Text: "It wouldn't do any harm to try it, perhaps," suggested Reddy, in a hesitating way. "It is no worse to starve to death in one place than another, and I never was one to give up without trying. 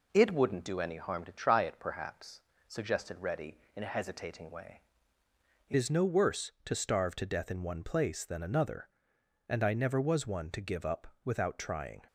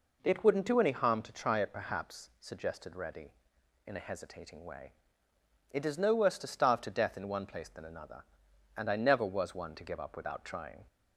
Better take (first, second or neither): second